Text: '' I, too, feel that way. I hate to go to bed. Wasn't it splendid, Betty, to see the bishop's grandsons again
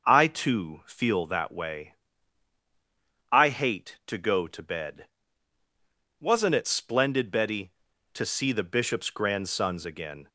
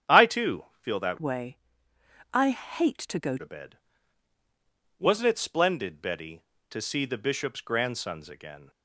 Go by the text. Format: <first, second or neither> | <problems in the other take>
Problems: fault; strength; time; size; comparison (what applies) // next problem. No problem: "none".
first | starts louder than the rest; strong; until 1.2 s; 9.5 dB // changes voice from "way" to "go"; from 1.1 to 3.3 s; 2.2 s long